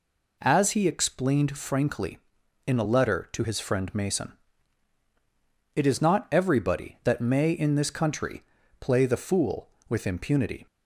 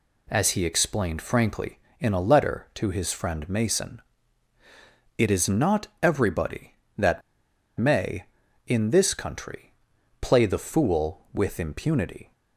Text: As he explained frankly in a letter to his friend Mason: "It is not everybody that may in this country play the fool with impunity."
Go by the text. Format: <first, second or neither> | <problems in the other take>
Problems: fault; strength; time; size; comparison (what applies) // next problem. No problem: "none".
first | pauses between "that" and "may"; noticeable; at 7.2 s; 0.56 s long // pauses between "country" and "play"; noticeable; at 9.7 s; 0.48 s long; also in the first